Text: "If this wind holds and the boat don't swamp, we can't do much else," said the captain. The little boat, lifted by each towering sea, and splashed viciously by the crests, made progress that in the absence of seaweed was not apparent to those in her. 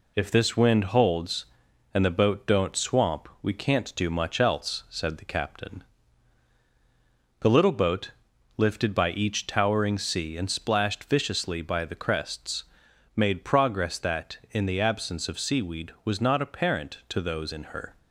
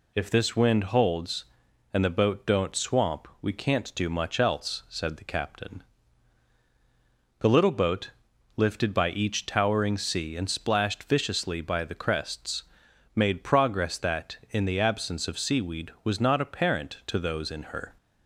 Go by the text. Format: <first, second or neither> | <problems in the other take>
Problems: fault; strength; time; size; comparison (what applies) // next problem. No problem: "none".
second | gets quieter; throughout; 3.5 dB